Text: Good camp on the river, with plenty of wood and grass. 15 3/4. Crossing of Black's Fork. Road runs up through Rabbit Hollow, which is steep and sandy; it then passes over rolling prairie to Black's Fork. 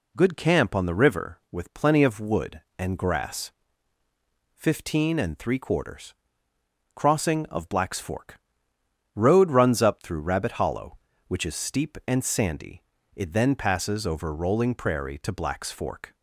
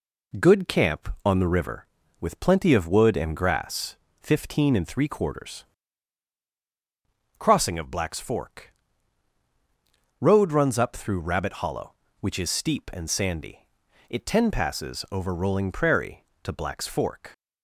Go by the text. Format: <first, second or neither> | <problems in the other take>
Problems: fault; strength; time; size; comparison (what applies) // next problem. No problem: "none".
first | says "ten" for "then"; at 14.2 s